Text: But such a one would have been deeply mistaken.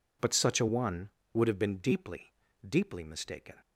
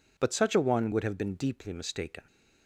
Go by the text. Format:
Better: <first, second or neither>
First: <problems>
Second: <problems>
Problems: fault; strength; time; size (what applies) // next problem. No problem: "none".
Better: second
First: says "deeply" twice; at 2.6 s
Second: none